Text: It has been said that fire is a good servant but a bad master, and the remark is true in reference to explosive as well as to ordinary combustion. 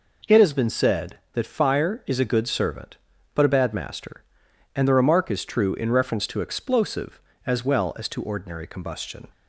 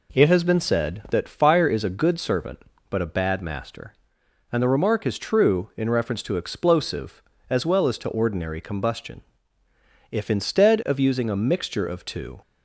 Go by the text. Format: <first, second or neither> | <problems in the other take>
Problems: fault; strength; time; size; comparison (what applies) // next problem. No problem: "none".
first | goes on to say "If instead of using a mixture of two"; strong; from 10.1 s on; 2.3 s long